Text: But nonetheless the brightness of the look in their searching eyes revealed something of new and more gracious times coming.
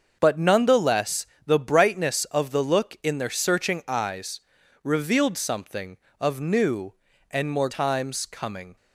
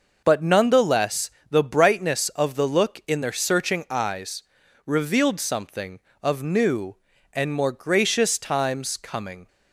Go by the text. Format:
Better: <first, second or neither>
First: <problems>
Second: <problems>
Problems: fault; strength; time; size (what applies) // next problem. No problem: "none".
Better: second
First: starts louder than the rest; until 1.2 s; 6.5 dB // pauses between "nonetheless" and "the"; slight; at 1.2 s; 0.20 s long // pauses between "eyes" and "revealed"; at 4.4 s; 0.42 s long // skips "gracious"; at 7.6 s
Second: pauses between "nonetheless" and "the"; slight; at 1.3 s; 0.20 s long // pauses between "eyes" and "revealed"; at 4.4 s; 0.42 s long